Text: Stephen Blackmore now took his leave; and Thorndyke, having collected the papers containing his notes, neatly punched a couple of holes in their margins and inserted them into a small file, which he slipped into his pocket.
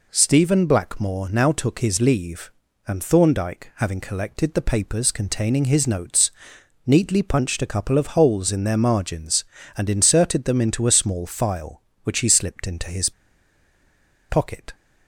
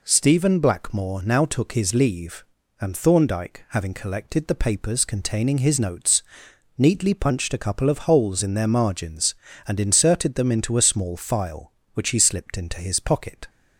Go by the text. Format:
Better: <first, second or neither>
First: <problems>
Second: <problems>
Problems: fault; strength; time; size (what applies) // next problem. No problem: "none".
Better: second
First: pauses between "his" and "pocket"; at 13.1 s; 1.1 s long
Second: none